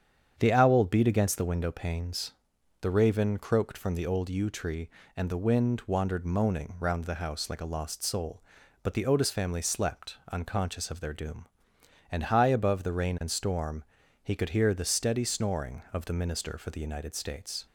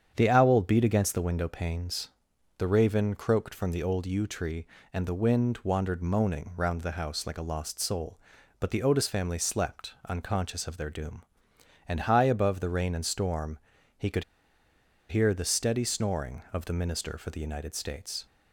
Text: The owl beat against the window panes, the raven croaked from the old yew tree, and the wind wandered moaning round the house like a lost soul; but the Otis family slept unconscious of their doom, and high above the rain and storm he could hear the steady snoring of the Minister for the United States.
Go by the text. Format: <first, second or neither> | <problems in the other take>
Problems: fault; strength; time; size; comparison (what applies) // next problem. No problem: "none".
first | starts louder than the rest; strong; until 1.1 s; 8 dB; strong in the first // pauses between "storm" and "he"; at 13.5 s; 0.40 s long; also in the first // pauses between "could" and "hear"; noticeable; at 14.2 s; 0.85 s long